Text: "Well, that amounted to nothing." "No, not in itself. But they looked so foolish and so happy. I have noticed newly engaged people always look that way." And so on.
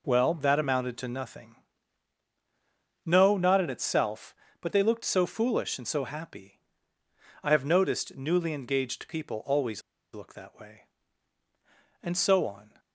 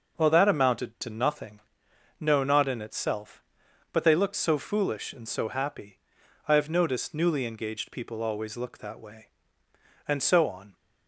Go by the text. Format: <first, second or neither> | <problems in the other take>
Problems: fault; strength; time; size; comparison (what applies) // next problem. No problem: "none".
second | pauses between "always" and "look"; slight; at 9.8 s; 0.31 s long